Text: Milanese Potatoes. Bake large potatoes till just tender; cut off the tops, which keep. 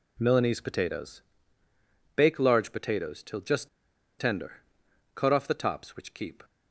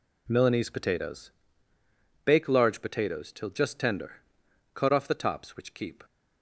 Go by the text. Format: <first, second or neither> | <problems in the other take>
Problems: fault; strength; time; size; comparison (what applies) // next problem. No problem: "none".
second | pauses between "just" and "tender"; noticeable; at 3.6 s; 0.50 s long